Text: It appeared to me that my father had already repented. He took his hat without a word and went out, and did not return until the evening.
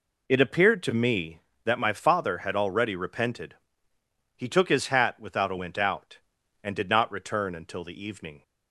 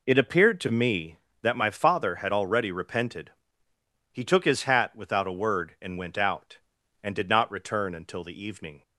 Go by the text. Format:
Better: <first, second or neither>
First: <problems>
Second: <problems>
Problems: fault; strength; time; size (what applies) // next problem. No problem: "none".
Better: second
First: skips "word and"; at 5.5 s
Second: none